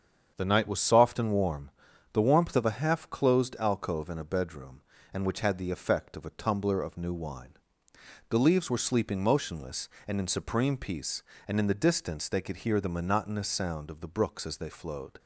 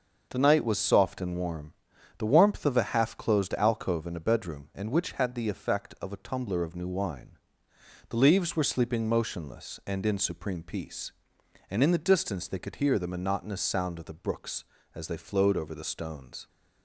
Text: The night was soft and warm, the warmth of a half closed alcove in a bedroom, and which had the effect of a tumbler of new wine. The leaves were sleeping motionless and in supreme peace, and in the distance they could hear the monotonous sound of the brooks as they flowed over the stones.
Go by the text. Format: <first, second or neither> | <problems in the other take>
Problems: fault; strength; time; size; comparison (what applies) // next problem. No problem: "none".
second | starts louder than the rest; strong; until 1.3 s; 7.5 dB; also in the second // stops before "over the stones"; at 15.1 s